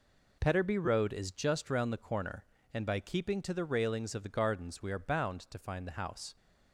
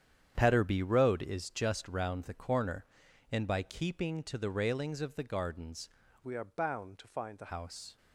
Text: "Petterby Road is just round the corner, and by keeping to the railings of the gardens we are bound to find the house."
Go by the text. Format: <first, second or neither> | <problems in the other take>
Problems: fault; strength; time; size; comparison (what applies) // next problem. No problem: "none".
first | starts louder than the rest; strong; until 1.3 s; 9 dB // changes voice from "we" to "the"; from 6.2 to 7.5 s; 1.3 s long